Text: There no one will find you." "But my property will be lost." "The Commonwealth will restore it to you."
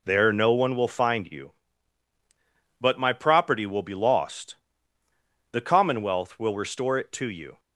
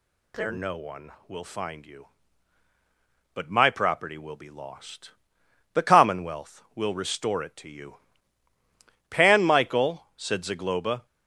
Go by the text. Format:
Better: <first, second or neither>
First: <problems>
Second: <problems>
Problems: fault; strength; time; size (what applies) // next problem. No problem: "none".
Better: first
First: none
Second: goes on to say "Pan Michael said Zagloba"; strong; from 9.0 s on; 1.9 s long